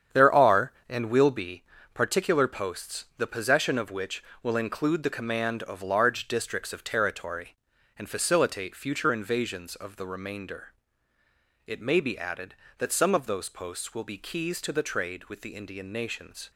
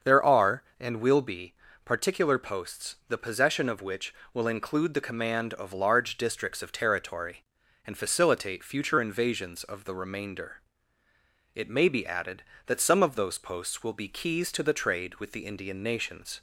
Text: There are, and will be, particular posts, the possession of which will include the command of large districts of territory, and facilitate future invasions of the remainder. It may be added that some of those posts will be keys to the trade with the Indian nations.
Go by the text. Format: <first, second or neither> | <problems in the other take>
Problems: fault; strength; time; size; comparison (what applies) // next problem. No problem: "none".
second | gets quieter; strong; throughout; 9 dB // starts louder than the rest; strong; until 1.2 s; 8.5 dB; also in the second